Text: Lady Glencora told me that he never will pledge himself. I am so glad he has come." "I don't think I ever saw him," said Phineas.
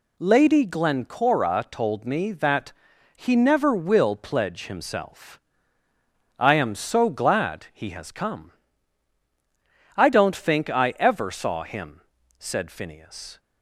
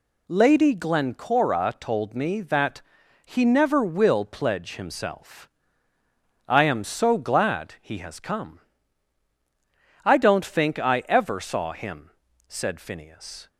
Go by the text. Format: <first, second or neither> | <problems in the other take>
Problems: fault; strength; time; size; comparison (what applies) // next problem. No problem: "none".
neither | pauses between "that" and "he"; the same in both